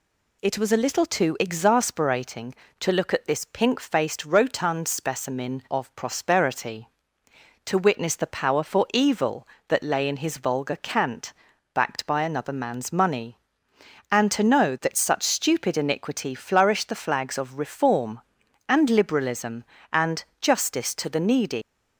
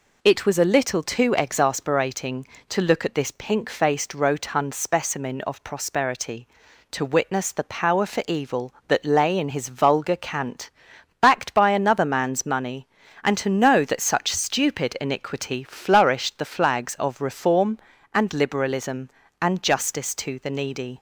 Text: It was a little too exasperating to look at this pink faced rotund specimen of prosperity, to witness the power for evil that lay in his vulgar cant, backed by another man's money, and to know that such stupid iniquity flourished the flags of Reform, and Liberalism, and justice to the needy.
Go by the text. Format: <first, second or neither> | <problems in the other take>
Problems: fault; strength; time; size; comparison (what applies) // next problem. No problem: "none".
second | pauses between "and" and "justice"; slight; at 20.2 s; 0.16 s long // leaves "needy" unfinished; at 21.6 s; 135 ms